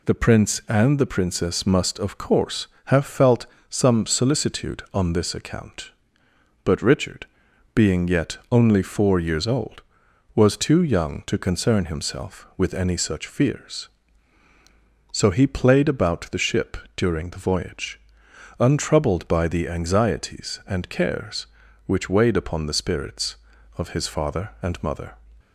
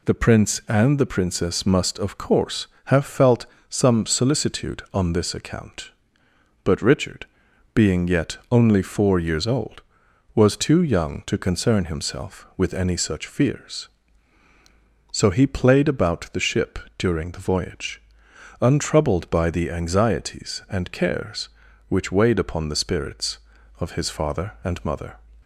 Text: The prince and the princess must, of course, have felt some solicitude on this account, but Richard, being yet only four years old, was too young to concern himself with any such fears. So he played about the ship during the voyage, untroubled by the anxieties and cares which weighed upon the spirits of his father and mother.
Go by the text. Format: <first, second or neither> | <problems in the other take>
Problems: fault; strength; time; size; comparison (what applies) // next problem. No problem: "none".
neither | pauses between "felt" and "some"; slight; the same in both // pauses between "ship" and "during"; slight; the same in both